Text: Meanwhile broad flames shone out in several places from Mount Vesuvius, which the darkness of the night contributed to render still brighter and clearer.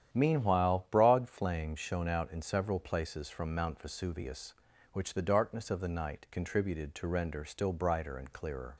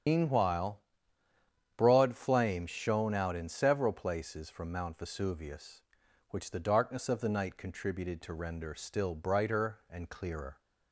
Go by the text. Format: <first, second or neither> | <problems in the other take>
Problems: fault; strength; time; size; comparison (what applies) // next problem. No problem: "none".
first | loses the start of "Meanwhile"; at 0.0 s; 110 ms // starts louder than the rest; strong; until 2.0 s; 9 dB; strong in the first // pauses between "Meanwhile" and "broad"; noticeable; at 0.8 s; 0.96 s long